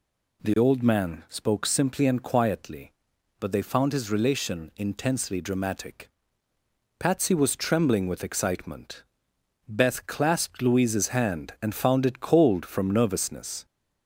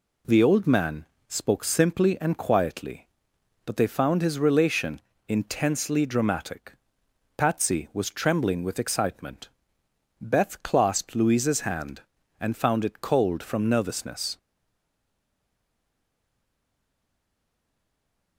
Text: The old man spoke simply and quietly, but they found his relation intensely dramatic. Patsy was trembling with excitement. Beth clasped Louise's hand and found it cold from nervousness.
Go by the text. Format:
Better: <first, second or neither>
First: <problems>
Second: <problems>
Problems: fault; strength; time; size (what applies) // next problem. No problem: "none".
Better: first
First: none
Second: pauses between "man" and "spoke"; slight; at 1.0 s; 0.24 s long // pauses between "relation" and "intensely"; slight; at 4.9 s; 0.28 s long // stays silent after the last word; strong; from 14.3 s on; 4.0 s long